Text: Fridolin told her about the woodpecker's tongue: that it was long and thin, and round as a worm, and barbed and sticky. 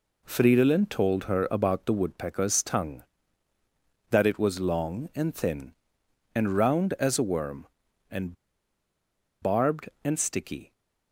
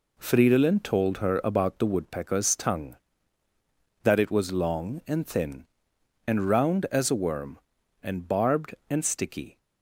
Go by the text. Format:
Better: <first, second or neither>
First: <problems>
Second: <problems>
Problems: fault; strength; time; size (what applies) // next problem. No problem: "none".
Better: second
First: pauses between "and" and "barbed"; at 8.3 s; 1.0 s long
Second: none